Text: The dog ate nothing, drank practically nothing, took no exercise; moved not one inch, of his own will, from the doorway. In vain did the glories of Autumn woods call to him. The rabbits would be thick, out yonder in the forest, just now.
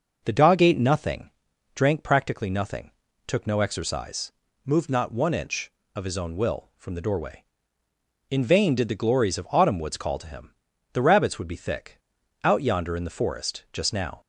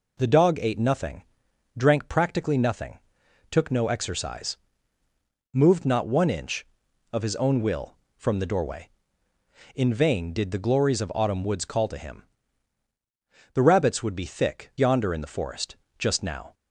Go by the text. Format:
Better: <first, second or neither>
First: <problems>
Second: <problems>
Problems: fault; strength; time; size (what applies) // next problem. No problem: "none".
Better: first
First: none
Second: skips "out"; at 14.7 s